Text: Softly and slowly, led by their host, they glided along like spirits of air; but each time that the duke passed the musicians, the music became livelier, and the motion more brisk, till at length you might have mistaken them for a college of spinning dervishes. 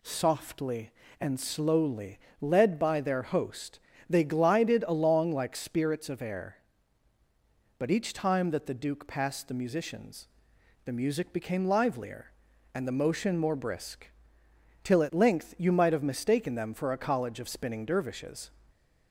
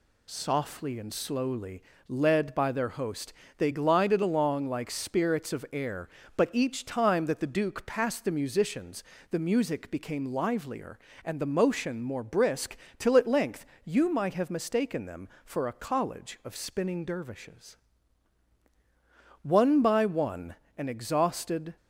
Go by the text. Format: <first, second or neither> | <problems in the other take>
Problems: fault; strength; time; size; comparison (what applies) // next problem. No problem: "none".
first | pauses between "length" and "you"; slight; at 13.6 s; 0.22 s long // goes on to say "One by one an exhausted"; strong; from 19.4 s on; 2.3 s long